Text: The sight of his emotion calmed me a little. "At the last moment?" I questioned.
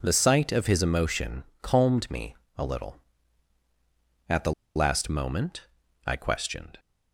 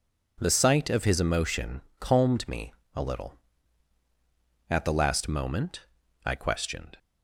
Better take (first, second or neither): second